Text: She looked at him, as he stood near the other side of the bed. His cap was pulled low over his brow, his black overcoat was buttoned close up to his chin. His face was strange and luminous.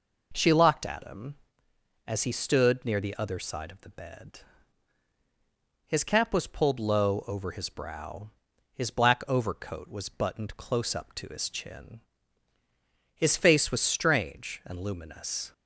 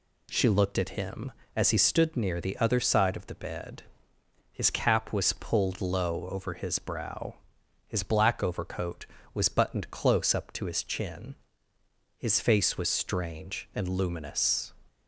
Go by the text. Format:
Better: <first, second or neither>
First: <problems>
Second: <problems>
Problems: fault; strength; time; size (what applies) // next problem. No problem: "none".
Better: second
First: says "locked" for "looked"; at 0.5 s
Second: none